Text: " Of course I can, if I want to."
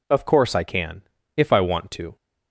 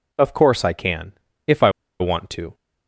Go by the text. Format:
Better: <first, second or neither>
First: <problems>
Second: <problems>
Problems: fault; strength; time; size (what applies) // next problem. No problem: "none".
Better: first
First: none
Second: pauses between "I" and "want"; slight; at 1.6 s; 0.30 s long